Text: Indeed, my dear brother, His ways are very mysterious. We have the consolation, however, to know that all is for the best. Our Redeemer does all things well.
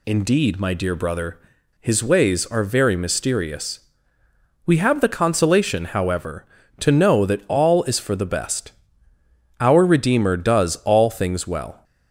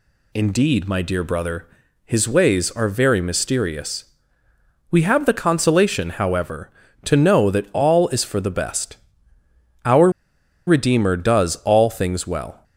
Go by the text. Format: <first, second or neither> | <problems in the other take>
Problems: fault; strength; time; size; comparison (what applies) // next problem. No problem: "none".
first | pauses between "Our" and "Redeemer"; noticeable; at 10.1 s; 0.56 s long